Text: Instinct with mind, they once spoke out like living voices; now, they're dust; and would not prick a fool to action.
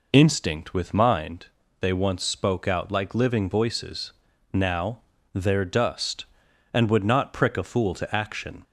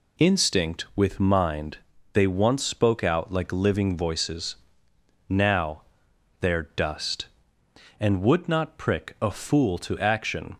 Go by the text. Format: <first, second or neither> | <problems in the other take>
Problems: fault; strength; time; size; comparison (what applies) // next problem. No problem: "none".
neither | none